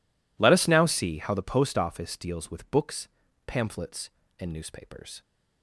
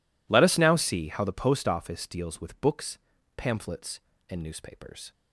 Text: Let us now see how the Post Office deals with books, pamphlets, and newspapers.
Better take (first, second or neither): neither